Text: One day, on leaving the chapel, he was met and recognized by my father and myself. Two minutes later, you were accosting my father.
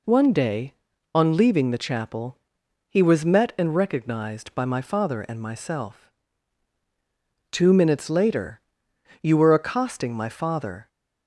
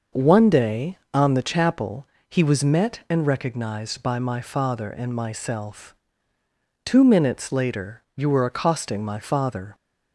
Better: first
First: none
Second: skips "leaving"; at 1.3 s

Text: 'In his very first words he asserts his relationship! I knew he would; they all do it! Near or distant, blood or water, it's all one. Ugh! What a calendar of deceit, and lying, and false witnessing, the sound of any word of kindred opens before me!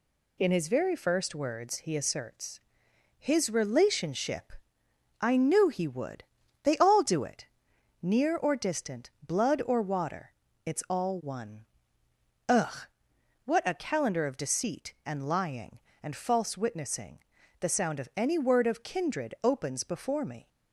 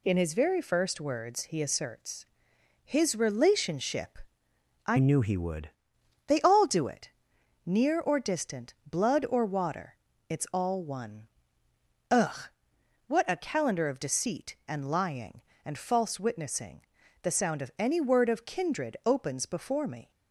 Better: first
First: pauses between "asserts" and "his"; noticeable; at 2.6 s; 0.60 s long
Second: pauses between "asserts" and "his"; noticeable; at 2.2 s; 0.60 s long // changes voice from "knew" to "would"; from 4.9 to 5.7 s; 0.8 s long

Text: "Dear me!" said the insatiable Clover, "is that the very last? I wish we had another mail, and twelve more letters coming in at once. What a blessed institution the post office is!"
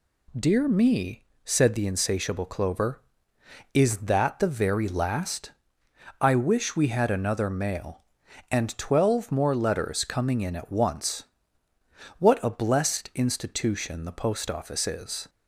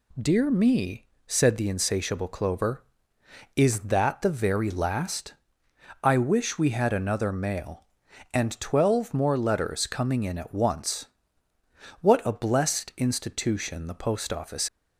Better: first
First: none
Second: stops before "is"; at 14.6 s

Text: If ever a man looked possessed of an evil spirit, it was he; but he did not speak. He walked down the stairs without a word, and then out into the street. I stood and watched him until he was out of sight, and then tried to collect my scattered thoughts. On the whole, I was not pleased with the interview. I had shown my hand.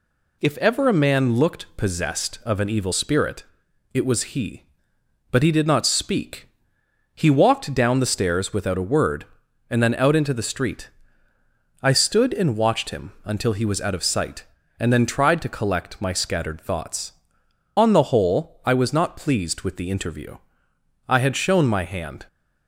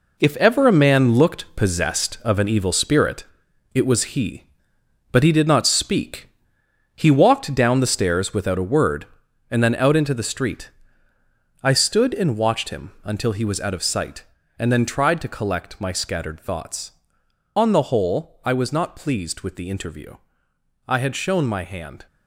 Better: first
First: none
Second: gets quieter; strong; throughout; 9 dB

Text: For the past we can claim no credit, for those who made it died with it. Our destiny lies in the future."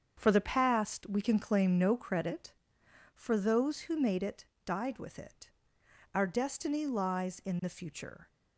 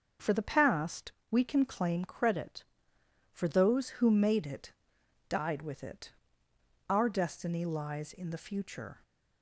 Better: first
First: starts louder than the rest; strong; until 1.1 s; 7 dB // pauses between "it" and "died"; slight; at 4.4 s; 0.18 s long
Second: starts louder than the rest; until 1.3 s; 6.5 dB // pauses between "past" and "we"; slight; at 1.1 s; 0.18 s long // skips "no"; at 2.0 s // pauses between "it" and "died"; noticeable; at 4.7 s; 0.59 s long

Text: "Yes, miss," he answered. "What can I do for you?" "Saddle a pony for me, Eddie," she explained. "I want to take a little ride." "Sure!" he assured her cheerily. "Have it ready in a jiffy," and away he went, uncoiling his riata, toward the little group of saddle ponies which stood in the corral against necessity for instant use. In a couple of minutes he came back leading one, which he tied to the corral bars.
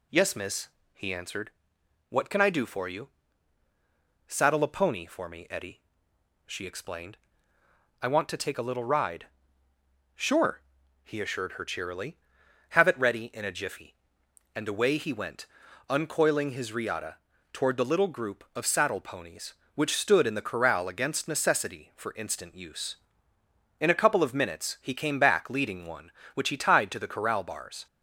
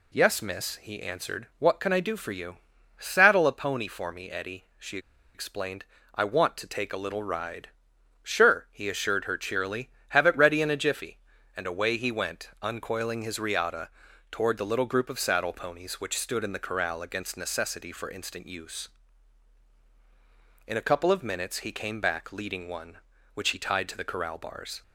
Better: first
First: none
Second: pauses between "she" and "explained"; slight; at 4.9 s; 0.35 s long

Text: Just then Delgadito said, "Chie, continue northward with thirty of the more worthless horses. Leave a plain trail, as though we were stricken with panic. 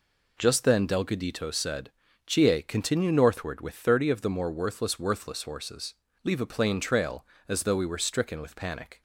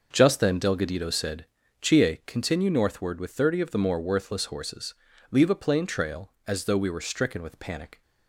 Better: second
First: says "worthless" twice; at 4.9 s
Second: none

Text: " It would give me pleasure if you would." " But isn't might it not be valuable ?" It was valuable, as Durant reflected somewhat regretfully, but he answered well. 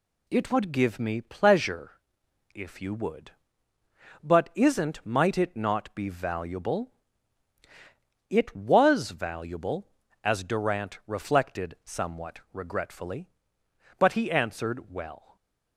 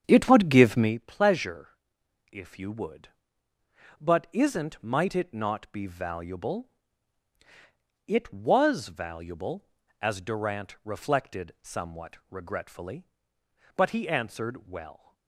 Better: first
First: pauses between "pleasure" and "if"; noticeable; at 1.9 s; 0.62 s long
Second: starts louder than the rest; strong; until 1.0 s; 8.5 dB // pauses between "pleasure" and "if"; noticeable; at 1.6 s; 0.62 s long

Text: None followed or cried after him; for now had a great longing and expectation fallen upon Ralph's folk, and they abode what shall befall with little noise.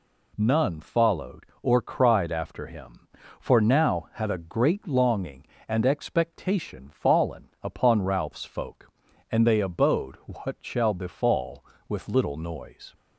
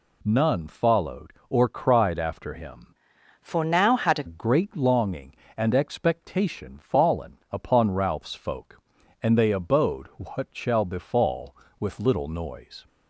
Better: first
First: none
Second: changes voice from "for" to "a"; from 3.4 to 4.2 s; 0.8 s long

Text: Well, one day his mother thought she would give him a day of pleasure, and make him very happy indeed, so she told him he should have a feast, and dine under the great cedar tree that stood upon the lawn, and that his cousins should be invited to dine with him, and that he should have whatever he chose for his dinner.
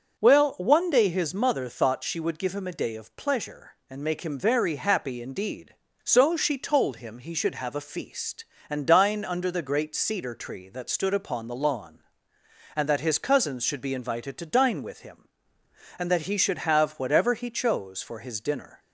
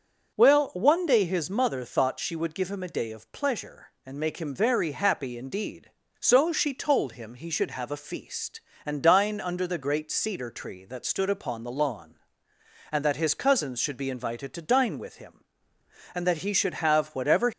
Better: first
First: starts louder than the rest; until 1.2 s; 6.5 dB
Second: starts louder than the rest; until 1.3 s; 6.5 dB // stops before "he chose for his dinner"; at 17.5 s

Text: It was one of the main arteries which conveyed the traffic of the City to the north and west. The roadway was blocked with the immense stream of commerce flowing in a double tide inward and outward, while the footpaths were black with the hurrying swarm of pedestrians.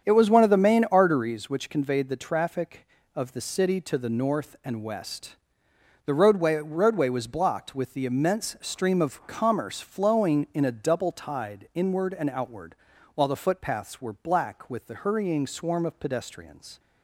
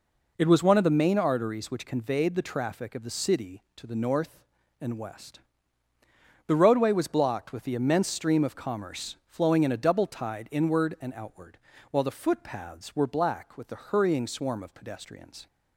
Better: second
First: starts louder than the rest; strong; until 1.0 s; 8 dB // says "roadway" twice; at 6.5 s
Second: none

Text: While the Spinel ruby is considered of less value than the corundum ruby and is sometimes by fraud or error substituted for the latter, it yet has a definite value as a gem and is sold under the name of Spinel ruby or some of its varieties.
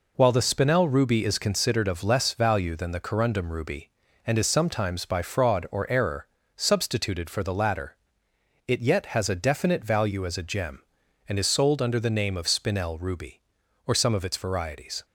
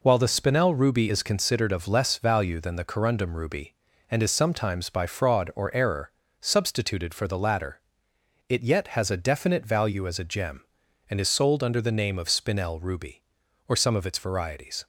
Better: neither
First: pauses between "error" and "substituted"; slight; at 6.2 s; 0.30 s long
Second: pauses between "error" and "substituted"; slight; at 6.1 s; 0.30 s long

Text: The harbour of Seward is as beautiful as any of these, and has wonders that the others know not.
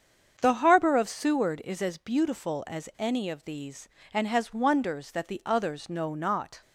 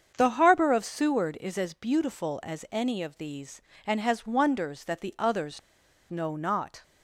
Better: first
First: starts louder than the rest; strong; until 1.4 s; 7 dB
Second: starts louder than the rest; strong; until 1.1 s; 7 dB // pauses between "others" and "know"; noticeable; at 5.6 s; 0.49 s long

